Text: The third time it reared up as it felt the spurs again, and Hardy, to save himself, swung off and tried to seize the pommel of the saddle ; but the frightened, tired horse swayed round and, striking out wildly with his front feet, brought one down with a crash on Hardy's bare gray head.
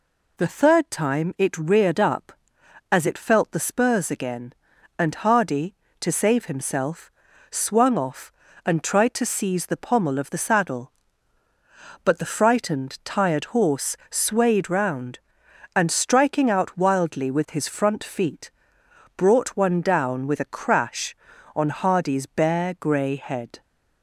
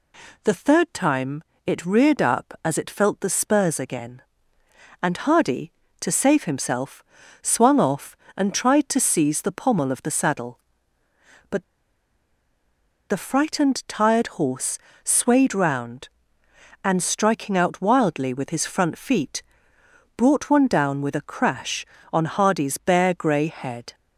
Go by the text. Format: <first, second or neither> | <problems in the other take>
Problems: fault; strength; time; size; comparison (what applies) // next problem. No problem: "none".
first | pauses between "time" and "it"; slight; at 1.4 s; 0.22 s long // pauses between "but" and "the"; strong; at 11.6 s; 1.4 s long // pauses between "horse" and "swayed"; slight; at 14.7 s; 0.26 s long; slight in the first